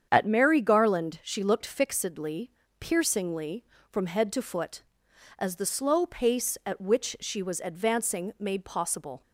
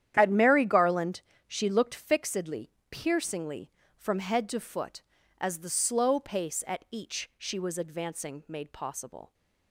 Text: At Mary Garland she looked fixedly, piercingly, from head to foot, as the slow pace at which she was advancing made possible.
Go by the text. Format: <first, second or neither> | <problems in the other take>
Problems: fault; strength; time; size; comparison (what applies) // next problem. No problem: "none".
first | starts louder than the rest; strong; until 1.1 s; 10.5 dB; strong in the first // pauses between "Garland" and "she"; slight; at 1.1 s; 0.26 s long // says "each" for "which"; at 6.8 s